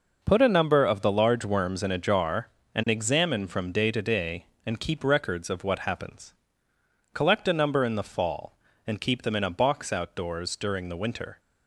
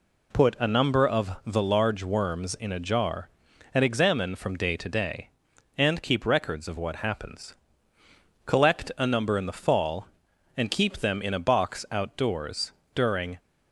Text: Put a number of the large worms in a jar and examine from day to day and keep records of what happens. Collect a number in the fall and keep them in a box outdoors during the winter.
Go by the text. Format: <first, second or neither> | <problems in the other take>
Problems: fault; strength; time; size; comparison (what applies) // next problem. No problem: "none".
first | pauses between "outdoors" and "during"; slight; at 12.7 s; 0.22 s long // stops before "the winter"; at 13.3 s